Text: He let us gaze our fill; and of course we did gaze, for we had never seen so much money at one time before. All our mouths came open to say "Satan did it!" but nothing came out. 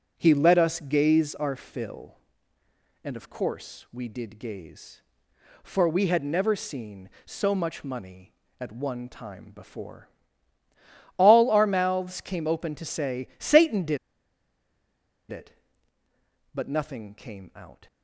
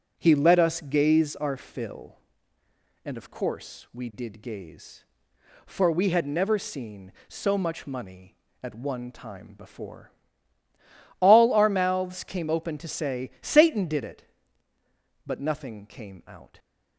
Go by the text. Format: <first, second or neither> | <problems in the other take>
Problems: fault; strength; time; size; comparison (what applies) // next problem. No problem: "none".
second | pauses between "did" and "it"; strong; at 13.9 s; 1.3 s long